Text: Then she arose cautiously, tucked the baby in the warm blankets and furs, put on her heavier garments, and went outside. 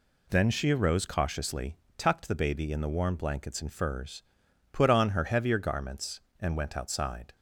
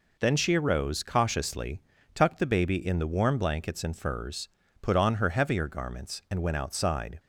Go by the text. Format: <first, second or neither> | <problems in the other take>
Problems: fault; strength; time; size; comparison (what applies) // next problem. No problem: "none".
neither | none